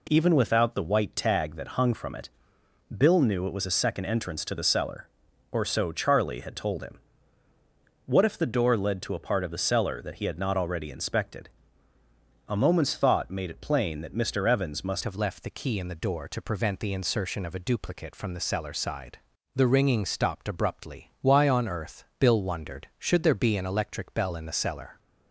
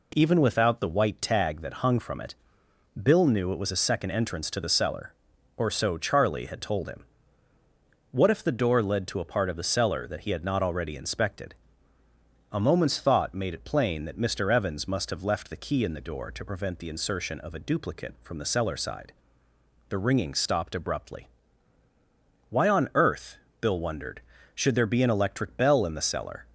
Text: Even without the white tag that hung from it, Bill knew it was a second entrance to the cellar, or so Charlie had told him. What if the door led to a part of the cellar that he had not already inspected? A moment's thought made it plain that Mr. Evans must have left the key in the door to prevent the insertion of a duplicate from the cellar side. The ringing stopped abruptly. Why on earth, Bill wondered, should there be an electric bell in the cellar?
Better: second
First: changes voice at "have"; from 15.0 s on; 9.9 s long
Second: none

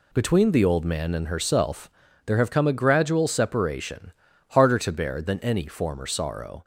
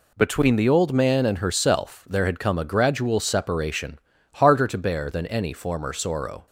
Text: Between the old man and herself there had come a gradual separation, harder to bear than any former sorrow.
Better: second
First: pauses between "herself" and "there"; slight; at 1.9 s; 0.36 s long // says "have" for "had"; at 2.3 s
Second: none

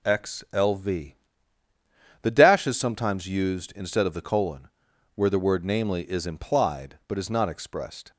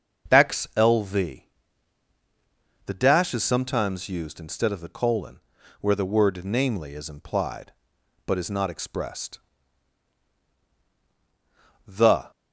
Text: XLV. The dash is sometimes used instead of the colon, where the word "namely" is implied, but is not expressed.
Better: first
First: none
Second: starts louder than the rest; until 1.3 s; 6.5 dB // goes on to say "The"; slight; from 11.8 s on; 0.44 s long

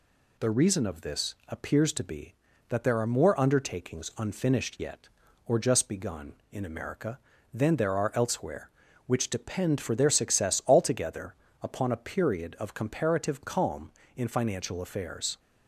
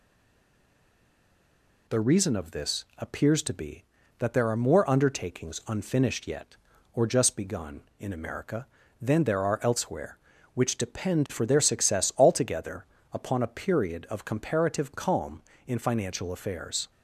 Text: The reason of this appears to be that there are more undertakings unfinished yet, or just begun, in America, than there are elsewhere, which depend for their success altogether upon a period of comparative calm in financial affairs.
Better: first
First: pauses between "altogether" and "upon"; slight; at 11.3 s; 0.28 s long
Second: stays silent before the first word; noticeable; until 1.8 s; 1.8 s long // pauses between "altogether" and "upon"; slight; at 12.8 s; 0.28 s long

